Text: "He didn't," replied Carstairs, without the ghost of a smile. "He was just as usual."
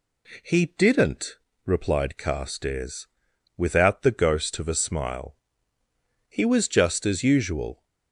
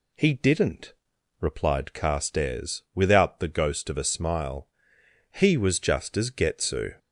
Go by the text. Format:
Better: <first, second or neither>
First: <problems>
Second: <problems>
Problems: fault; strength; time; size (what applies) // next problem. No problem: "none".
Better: first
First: none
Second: says "getsu" for "usual"; at 6.2 s